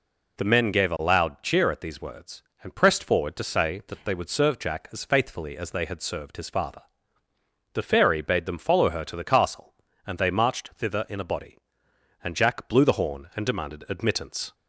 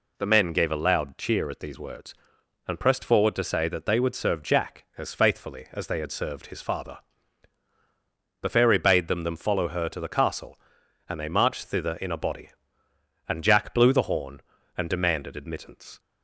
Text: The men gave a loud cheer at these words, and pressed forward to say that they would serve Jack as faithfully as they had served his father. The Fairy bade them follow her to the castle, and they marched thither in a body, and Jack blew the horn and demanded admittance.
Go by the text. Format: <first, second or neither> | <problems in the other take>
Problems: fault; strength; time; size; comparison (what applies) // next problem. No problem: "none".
first | says "them" twice; at 9.2 s